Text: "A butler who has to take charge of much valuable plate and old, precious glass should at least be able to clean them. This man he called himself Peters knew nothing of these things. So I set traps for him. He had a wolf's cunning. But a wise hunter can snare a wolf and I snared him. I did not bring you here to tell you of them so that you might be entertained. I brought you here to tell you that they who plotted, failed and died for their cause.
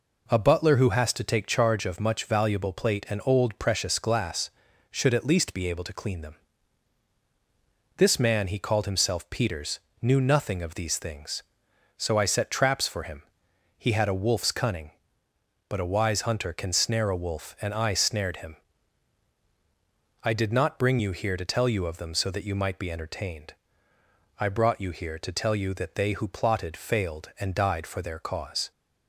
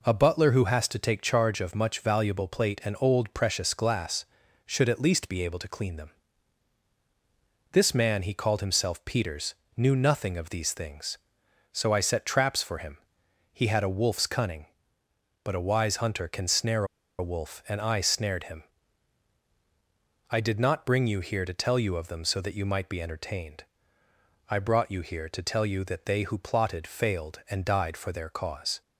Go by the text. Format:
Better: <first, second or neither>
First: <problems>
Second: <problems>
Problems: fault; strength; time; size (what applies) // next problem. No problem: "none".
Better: first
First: pauses between "Peters" and "knew"; slight; at 9.7 s; 0.24 s long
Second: pauses between "Peters" and "knew"; slight; at 9.5 s; 0.24 s long // pauses between "snare" and "a"; slight; at 16.8 s; 0.34 s long